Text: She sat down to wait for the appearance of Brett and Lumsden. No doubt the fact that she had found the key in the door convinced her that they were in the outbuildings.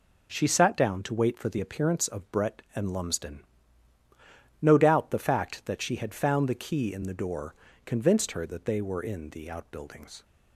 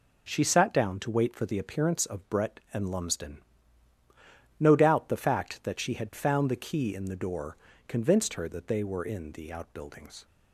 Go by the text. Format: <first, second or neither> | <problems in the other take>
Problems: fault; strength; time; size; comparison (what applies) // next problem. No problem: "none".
neither | pauses between "door" and "convinced"; slight; the same in both